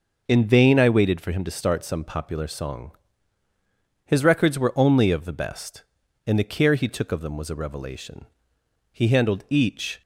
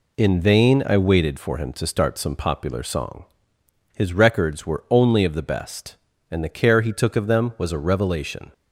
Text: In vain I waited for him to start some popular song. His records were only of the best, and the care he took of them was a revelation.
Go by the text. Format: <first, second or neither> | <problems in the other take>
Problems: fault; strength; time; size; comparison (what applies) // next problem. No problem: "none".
second | goes on to say "He handled each"; noticeable; from 8.9 s on; 1.1 s long